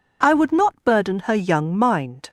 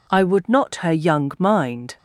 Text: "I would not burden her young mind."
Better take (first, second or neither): first